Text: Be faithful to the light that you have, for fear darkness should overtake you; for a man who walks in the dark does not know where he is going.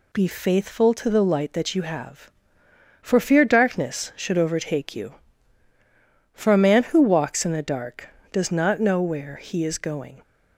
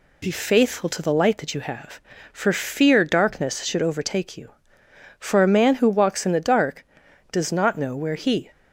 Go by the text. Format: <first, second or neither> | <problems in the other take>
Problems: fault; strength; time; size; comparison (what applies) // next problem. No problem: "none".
first | stops before "is going"; at 8.5 s